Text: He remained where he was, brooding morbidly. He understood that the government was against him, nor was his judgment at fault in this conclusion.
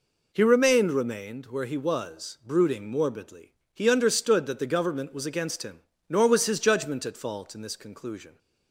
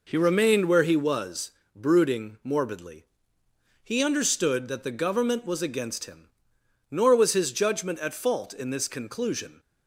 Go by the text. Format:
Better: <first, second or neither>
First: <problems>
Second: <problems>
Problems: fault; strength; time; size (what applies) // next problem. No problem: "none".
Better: second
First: says "remained" twice; at 0.9 s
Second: none